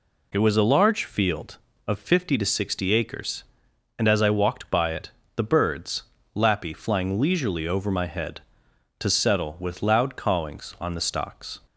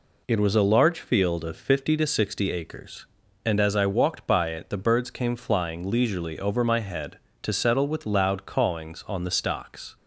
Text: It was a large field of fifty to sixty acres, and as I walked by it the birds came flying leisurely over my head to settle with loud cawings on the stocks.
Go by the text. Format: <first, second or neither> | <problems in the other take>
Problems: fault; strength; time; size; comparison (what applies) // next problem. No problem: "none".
second | pauses between "it" and "the"; slight; at 5.1 s; 0.24 s long // says "lappy" for "came"; at 6.3 s